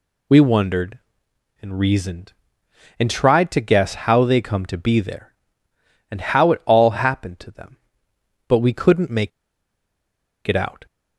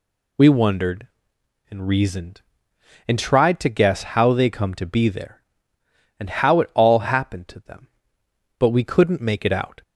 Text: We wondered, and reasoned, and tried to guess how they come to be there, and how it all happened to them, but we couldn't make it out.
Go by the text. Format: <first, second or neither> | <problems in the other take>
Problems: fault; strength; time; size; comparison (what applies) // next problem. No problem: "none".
second | pauses between "make" and "it"; at 9.3 s; 1.1 s long